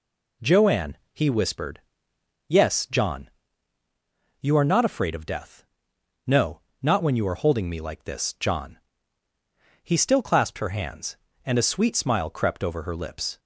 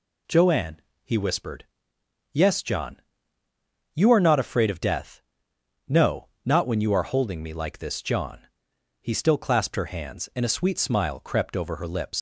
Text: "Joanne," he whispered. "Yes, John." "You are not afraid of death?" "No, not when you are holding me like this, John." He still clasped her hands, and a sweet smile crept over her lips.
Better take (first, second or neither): first